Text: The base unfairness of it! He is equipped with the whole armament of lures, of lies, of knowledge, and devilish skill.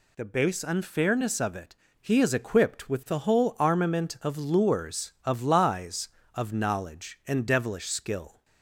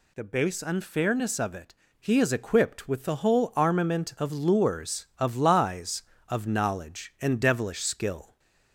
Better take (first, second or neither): second